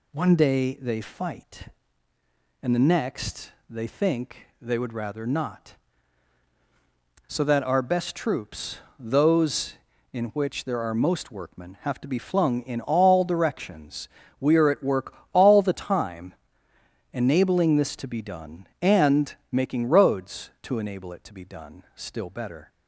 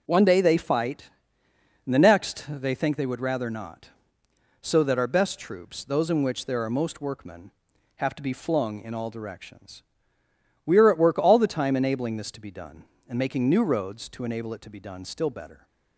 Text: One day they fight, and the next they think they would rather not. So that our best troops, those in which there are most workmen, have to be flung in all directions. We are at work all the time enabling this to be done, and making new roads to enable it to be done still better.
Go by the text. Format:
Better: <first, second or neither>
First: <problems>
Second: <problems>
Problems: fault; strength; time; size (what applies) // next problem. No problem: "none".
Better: second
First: pauses between "next" and "they"; slight; at 3.5 s; 0.18 s long // pauses between "work" and "all"; slight; at 15.1 s; 0.18 s long // pauses between "time" and "enabling"; noticeable; at 16.3 s; 0.80 s long // pauses between "and" and "making"; slight; at 19.3 s; 0.16 s long // skips "new"; at 19.8 s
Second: none